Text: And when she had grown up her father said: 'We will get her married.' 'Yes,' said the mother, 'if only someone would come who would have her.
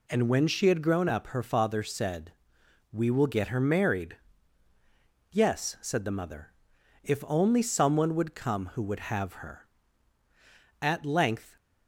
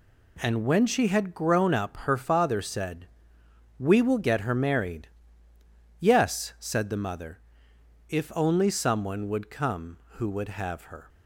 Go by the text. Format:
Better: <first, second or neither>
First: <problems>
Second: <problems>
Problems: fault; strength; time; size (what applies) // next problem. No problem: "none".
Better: second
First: goes on to say "At length"; noticeable; from 10.8 s on; 0.74 s long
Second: none